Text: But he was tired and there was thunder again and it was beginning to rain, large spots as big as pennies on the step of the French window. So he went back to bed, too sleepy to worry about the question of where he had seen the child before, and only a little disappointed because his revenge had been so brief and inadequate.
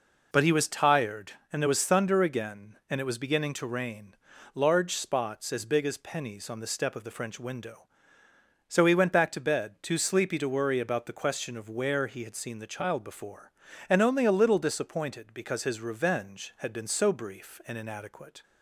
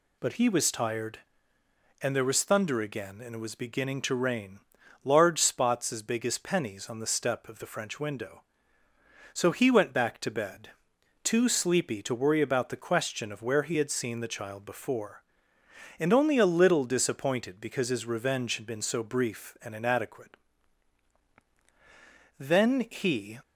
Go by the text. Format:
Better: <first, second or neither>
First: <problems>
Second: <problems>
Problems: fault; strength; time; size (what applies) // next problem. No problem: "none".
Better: first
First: none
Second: goes on to say "Then he"; noticeable; from 22.3 s on; 1.0 s long